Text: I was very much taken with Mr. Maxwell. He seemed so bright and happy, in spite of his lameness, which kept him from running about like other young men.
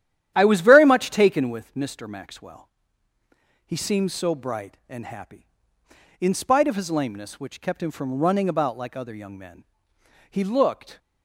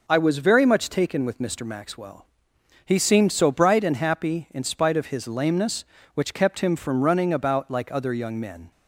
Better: second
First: starts louder than the rest; strong; until 1.3 s; 11 dB // goes on to say "He looked"; noticeable; from 10.3 s on; 0.68 s long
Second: none

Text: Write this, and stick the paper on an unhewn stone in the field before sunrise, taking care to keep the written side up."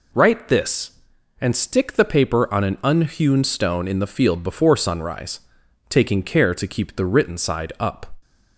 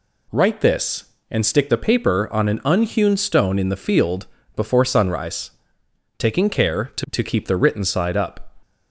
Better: first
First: none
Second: pauses between "field" and "before"; slight; at 4.2 s; 0.28 s long // says "to" twice; at 7.0 s

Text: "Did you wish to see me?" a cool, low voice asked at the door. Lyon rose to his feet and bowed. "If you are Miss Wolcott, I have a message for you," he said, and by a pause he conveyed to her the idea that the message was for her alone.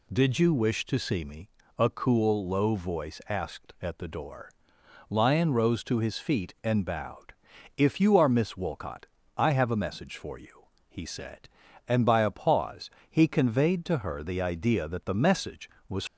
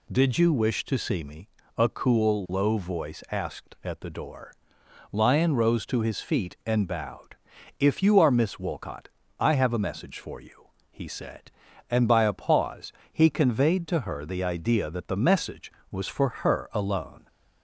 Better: second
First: pauses between "pause" and "he"; slight; at 12.8 s; 0.22 s long // stops before "for her alone"; at 16.0 s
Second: pauses between "pause" and "he"; slight; at 12.9 s; 0.22 s long

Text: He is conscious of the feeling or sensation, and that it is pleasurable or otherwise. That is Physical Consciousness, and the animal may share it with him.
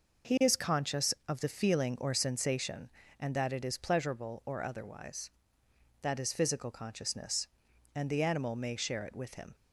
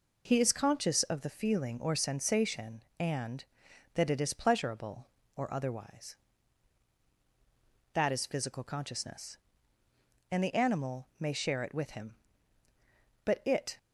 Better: first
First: none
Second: goes on to say "But it"; from 13.2 s on; 0.50 s long

